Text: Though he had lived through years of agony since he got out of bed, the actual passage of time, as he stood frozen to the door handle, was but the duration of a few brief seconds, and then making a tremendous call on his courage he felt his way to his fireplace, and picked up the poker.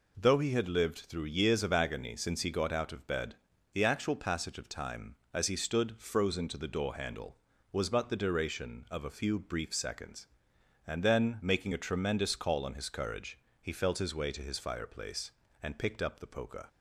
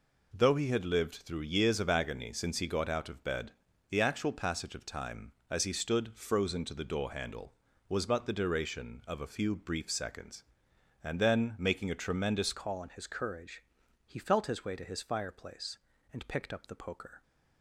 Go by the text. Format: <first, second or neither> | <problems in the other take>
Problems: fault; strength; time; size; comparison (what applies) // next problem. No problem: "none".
first | changes voice at "call"; from 12.5 s on; 4.7 s long // pauses between "courage" and "he"; at 13.6 s; 0.44 s long; slight in the first